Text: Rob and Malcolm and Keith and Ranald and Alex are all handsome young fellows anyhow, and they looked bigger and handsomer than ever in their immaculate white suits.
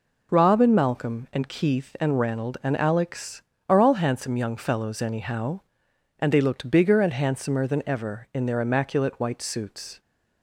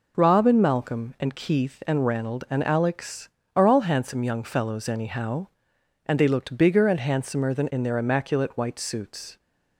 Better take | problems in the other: first | skips "ever"; at 7.7 s

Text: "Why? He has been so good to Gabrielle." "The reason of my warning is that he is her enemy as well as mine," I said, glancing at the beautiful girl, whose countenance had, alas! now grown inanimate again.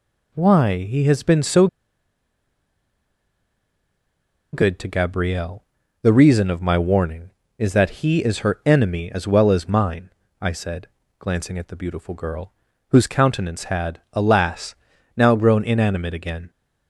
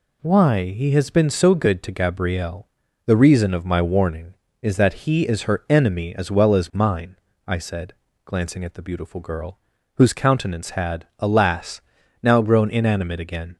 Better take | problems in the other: second | pauses between "so" and "good"; strong; at 1.6 s; 2.8 s long

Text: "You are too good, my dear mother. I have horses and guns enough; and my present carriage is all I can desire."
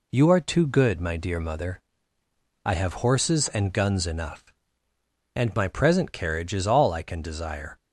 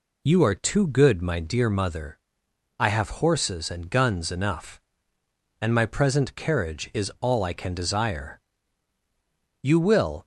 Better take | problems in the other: first | goes on to say "You will"; noticeable; from 9.6 s on; 0.62 s long

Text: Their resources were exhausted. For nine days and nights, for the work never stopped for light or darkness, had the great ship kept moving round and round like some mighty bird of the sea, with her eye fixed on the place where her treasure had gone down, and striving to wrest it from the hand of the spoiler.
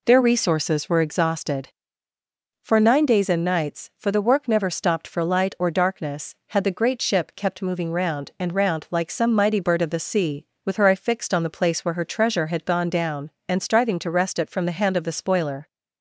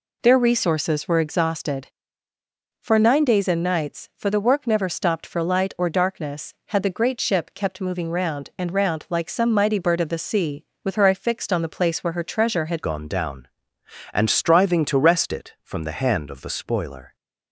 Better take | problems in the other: first | changes voice at "gone"; from 12.8 s on; 4.3 s long

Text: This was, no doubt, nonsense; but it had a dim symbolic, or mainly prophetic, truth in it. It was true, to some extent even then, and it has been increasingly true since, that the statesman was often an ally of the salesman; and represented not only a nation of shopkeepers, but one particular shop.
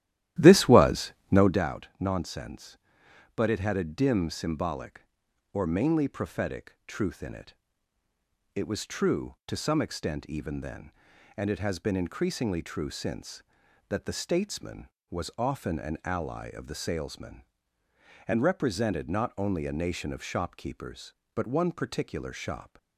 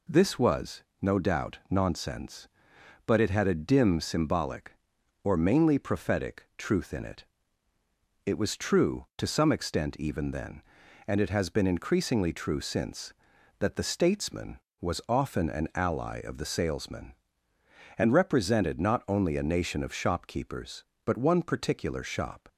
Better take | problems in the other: second | starts louder than the rest; strong; until 1.7 s; 13.5 dB

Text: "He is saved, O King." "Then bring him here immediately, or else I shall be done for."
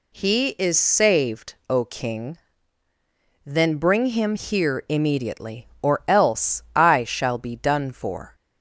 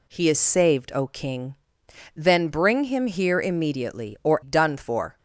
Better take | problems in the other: first | skips "else I shall be"; at 4.4 s

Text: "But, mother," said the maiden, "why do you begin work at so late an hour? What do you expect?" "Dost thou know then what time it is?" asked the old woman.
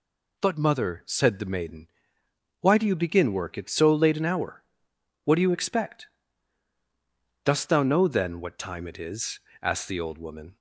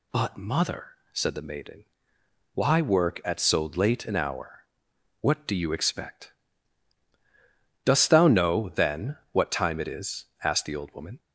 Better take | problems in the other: first | skips "do you begin"; at 2.8 s

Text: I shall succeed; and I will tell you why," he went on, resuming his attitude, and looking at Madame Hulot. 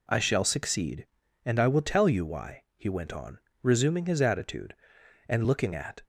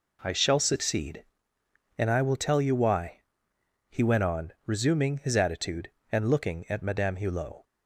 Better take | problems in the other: second | stops before "Madame Hulot"; at 6.0 s

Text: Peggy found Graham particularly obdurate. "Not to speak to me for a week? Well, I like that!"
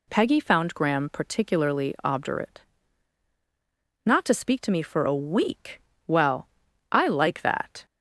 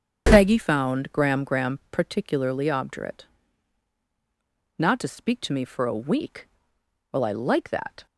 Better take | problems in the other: first | starts louder than the rest; strong; until 1.3 s; 8.5 dB // says "Graham" twice; at 1.4 s

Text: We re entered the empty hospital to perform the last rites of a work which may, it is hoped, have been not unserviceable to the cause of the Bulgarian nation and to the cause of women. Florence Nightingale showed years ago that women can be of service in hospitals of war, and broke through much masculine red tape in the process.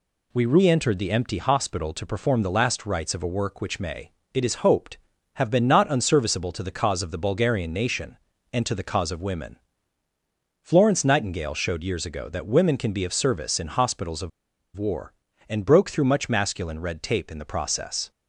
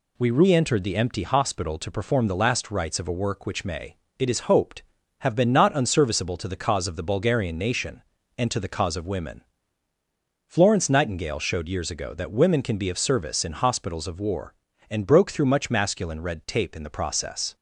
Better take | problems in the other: second | pauses between "of" and "war"; noticeable; at 14.3 s; 0.46 s long

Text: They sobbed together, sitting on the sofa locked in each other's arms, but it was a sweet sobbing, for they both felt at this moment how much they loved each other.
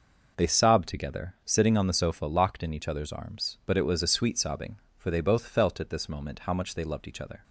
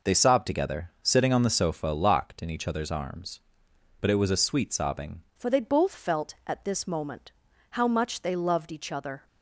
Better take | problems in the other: first | changes voice at "for"; from 5.3 s on; 3.9 s long // pauses between "moment" and "how"; at 7.3 s; 0.38 s long

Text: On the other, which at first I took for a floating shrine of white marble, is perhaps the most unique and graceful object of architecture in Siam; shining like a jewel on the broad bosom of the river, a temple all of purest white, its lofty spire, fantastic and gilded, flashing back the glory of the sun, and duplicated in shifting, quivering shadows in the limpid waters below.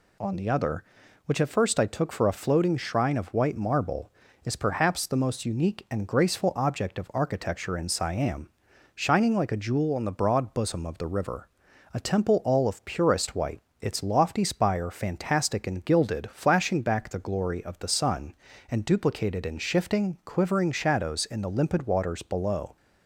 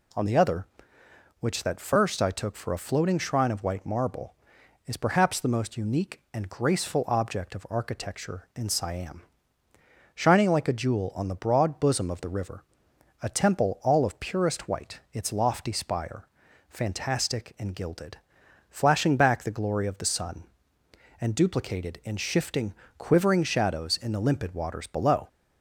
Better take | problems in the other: first | says "that" for "at"; at 1.6 s

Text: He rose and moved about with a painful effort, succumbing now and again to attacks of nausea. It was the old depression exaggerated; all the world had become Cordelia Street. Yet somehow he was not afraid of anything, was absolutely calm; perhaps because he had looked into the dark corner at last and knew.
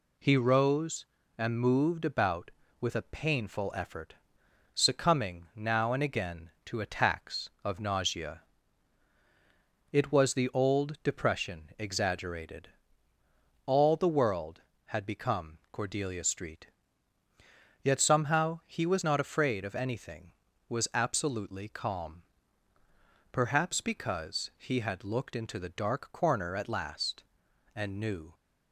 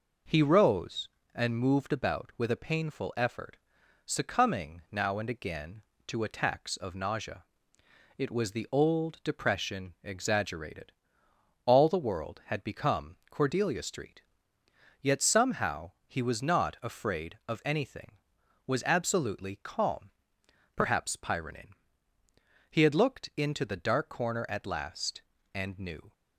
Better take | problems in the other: first | pauses between "somehow" and "he"; slight; at 15.9 s; 0.16 s long // says "pyronin" for "because"; at 21.1 s

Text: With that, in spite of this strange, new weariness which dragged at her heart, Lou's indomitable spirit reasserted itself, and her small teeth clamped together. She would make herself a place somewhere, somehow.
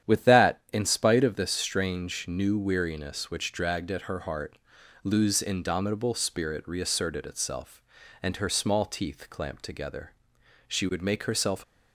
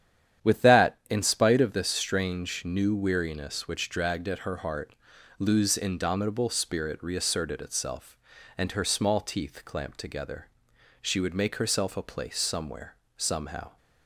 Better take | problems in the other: second | starts louder than the rest; strong; until 1.1 s; 9.5 dB; strong in the second // stops before "a place somewhere somehow"; at 11.6 s

